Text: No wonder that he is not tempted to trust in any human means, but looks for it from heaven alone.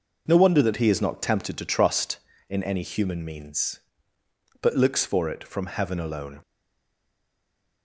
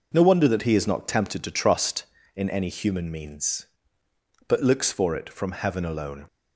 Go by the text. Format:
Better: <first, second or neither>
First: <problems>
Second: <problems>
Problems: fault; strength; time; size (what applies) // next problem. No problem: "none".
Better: second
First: stays silent after the last word; noticeable; from 6.4 s on; 1.4 s long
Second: none